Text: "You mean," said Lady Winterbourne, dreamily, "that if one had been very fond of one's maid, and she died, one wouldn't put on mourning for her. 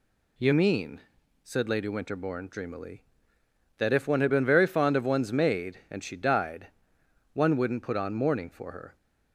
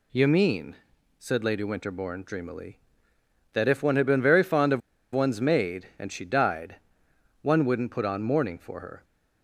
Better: first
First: none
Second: pauses between "of" and "one's"; slight; at 4.8 s; 0.33 s long

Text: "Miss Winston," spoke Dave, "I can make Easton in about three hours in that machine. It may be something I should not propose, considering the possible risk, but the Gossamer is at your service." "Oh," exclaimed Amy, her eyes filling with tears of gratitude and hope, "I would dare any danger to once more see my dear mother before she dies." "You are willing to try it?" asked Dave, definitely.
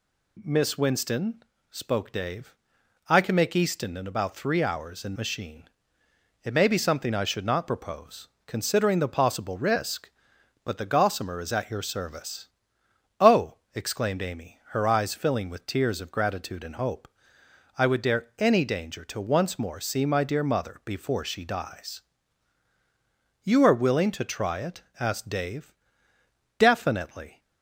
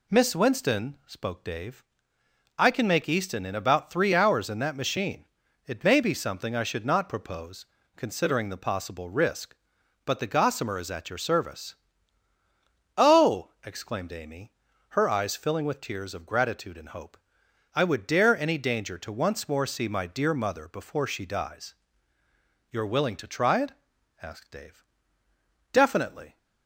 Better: second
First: skips "that"; at 5.1 s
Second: none

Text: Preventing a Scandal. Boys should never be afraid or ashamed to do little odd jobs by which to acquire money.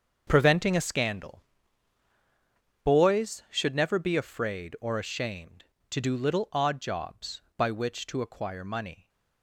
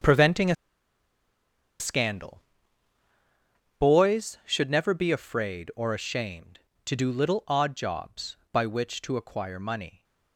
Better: first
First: starts louder than the rest; until 1.2 s; 7 dB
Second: starts louder than the rest; until 2.3 s; 7 dB // pauses between "a" and "Scandal"; strong; at 0.5 s; 1.2 s long

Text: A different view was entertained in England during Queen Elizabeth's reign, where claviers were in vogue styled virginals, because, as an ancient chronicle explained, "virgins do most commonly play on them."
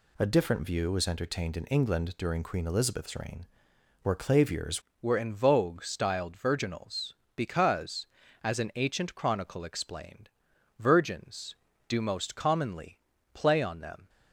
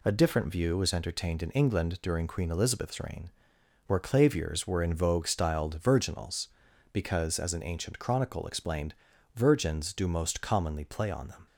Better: second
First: changes voice at "were"; from 5.0 s on; 9.0 s long // pauses between "commonly" and "play"; slight; at 12.9 s; 0.34 s long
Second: none

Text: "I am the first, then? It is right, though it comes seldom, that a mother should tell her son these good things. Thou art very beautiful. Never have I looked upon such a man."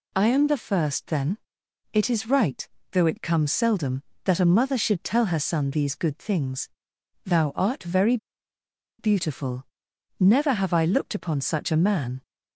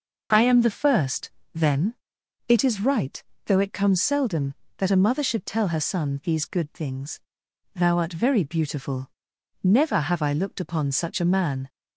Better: second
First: pauses between "very" and "beautiful"; noticeable; at 8.1 s; 0.82 s long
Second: none

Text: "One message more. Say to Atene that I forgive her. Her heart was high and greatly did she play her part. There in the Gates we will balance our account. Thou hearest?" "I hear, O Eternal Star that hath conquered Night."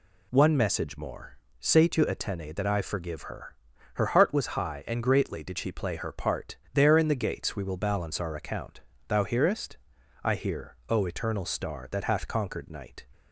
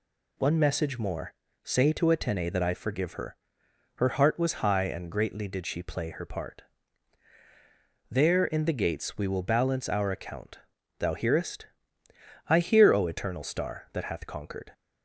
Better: first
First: none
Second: stops before "Night"; at 14.7 s

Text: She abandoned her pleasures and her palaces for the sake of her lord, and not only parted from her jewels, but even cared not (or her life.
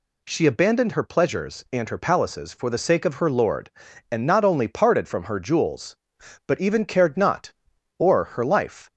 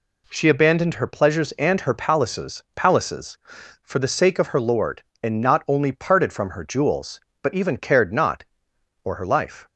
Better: first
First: none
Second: says "palaces" twice; at 2.7 s

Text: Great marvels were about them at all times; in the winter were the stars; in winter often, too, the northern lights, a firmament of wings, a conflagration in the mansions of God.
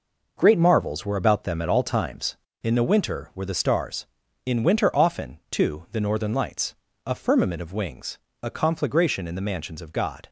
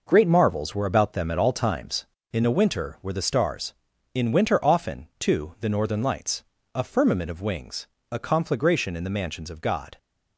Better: neither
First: none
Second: none

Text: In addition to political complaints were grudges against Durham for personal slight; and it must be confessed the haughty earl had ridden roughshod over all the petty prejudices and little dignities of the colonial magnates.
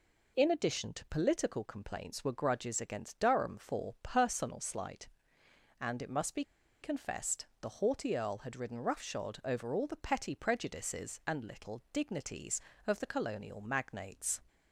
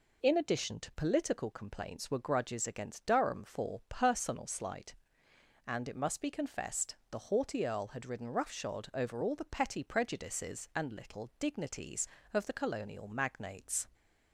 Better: second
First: pauses between "be" and "confessed"; at 6.4 s; 0.39 s long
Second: none

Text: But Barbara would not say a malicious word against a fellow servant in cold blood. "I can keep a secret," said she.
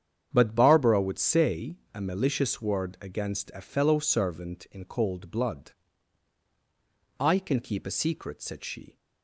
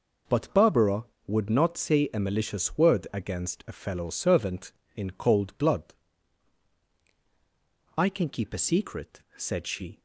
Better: second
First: starts louder than the rest; strong; until 1.3 s; 8.5 dB // skips "not"; at 1.1 s // pauses between "say" and "a"; slight; at 1.7 s; 0.16 s long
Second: none

